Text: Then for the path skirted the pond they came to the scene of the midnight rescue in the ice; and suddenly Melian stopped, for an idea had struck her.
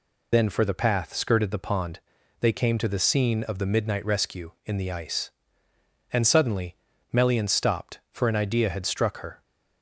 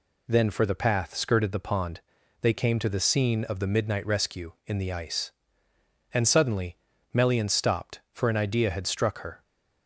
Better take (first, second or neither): second